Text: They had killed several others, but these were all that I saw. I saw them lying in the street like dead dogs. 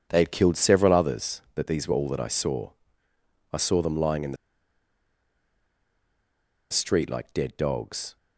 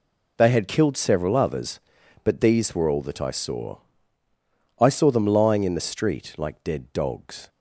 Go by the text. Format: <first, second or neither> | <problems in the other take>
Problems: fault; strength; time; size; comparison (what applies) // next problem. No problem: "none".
second | pauses between "the" and "street"; strong; at 4.3 s; 2.3 s long